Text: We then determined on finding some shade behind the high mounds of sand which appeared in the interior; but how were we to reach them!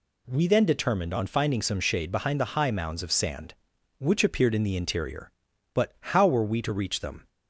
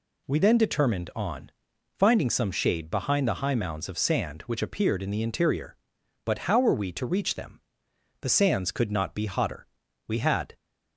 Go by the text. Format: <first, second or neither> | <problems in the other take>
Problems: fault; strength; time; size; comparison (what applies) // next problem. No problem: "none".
first | pauses between "on" and "finding"; noticeable; at 1.4 s; 0.48 s long // goes on to say "The sands could not be hotter We had"; strong; from 8.2 s on; 2.3 s long